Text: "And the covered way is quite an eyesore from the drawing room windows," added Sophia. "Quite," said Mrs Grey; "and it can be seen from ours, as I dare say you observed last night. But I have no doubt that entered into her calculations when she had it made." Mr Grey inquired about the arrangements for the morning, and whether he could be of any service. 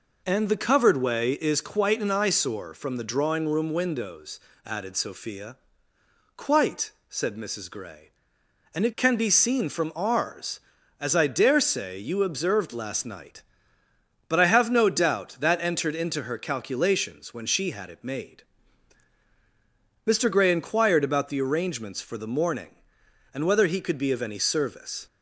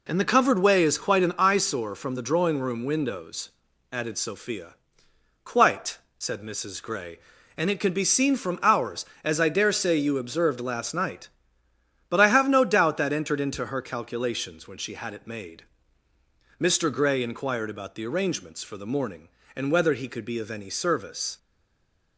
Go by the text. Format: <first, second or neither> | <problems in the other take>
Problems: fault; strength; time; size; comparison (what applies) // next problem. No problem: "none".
first | stays silent after the last word; slight; from 21.3 s on; 0.8 s long